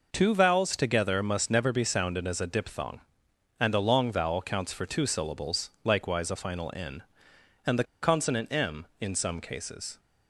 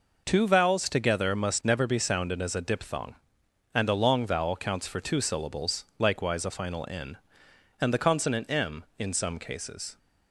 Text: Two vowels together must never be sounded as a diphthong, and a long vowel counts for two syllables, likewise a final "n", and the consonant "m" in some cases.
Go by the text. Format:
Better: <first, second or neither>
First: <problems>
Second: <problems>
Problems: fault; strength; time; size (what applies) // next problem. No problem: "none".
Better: second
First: pauses between "the" and "consonant"; slight; at 7.8 s; 0.19 s long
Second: none